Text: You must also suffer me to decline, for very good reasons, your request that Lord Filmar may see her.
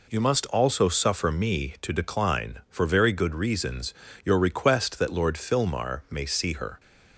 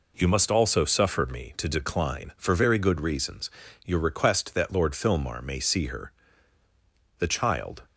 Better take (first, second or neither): first